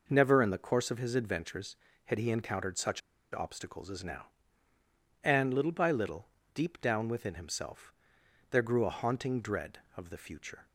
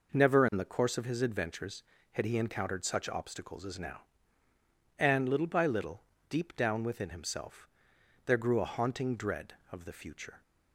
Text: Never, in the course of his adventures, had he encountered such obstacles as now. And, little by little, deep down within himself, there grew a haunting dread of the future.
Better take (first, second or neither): second